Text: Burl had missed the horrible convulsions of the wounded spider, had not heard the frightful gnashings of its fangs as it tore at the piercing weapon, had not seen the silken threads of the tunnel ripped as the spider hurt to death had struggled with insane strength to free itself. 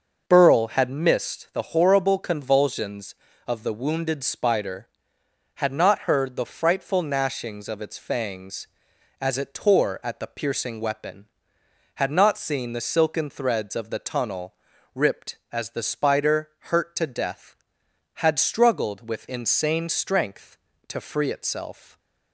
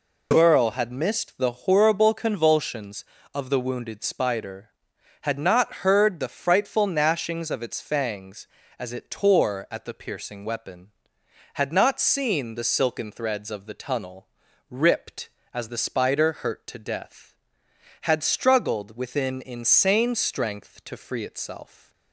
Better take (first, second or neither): first